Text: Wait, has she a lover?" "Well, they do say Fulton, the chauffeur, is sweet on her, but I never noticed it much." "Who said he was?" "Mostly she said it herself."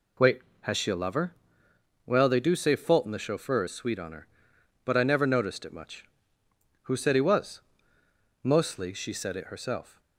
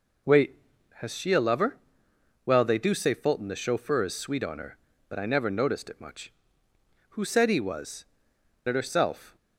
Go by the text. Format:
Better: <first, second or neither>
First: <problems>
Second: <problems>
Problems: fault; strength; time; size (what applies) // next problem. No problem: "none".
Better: first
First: none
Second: skips "Mostly she said"; at 8.3 s